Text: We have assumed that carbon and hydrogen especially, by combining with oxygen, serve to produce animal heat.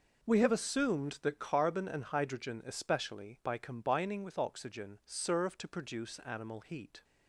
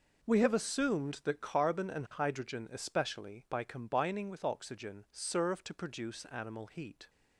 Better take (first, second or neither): neither